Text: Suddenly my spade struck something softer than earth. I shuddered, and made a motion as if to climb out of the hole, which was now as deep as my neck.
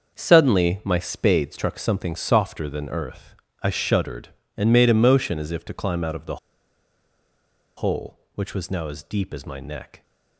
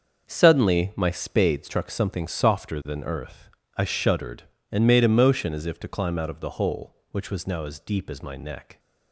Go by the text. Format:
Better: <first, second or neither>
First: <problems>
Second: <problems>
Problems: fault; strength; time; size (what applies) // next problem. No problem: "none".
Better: second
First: starts louder than the rest; until 1.2 s; 6.5 dB // pauses between "the" and "hole"; strong; at 6.3 s; 1.4 s long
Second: starts louder than the rest; until 1.3 s; 6.5 dB